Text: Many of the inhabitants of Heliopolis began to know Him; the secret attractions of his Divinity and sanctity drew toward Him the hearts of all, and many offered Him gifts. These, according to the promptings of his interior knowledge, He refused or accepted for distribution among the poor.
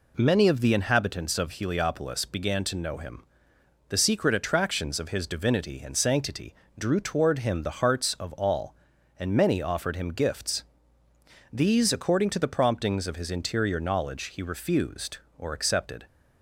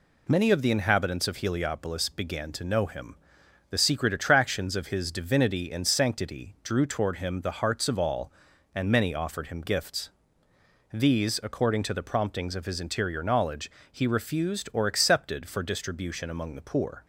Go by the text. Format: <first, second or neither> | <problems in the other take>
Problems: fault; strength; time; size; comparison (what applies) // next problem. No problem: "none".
second | pauses between "sanctity" and "drew"; slight; at 6.5 s; 0.24 s long // stops before "for distribution among the poor"; at 16.0 s